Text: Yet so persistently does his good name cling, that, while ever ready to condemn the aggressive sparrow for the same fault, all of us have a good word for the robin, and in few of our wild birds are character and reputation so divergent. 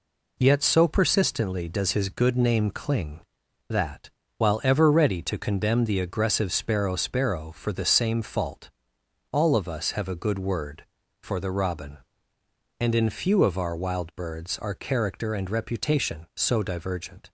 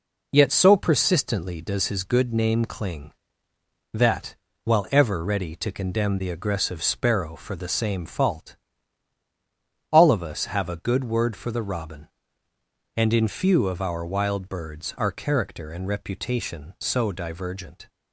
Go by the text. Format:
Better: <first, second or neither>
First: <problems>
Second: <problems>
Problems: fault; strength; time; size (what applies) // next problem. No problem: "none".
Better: second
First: says "sparrow" twice; at 6.9 s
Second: none